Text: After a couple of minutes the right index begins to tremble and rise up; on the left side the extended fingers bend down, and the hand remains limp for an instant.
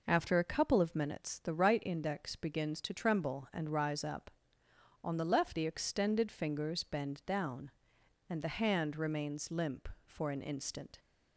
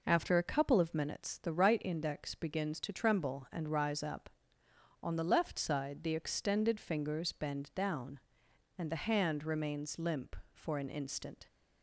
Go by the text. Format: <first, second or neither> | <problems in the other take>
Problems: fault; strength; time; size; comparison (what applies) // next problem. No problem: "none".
second | skips "side"; at 5.5 s